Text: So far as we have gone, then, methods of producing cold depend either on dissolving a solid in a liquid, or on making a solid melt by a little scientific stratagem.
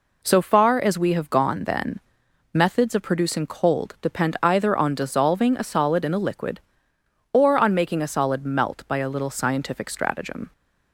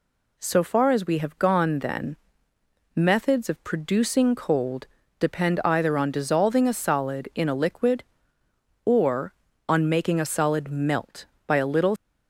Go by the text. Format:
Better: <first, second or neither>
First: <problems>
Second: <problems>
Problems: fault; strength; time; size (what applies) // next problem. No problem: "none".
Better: first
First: none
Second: pauses between "cold" and "depend"; slight; at 4.8 s; 0.34 s long // stops before "scientific stratagem"; at 11.9 s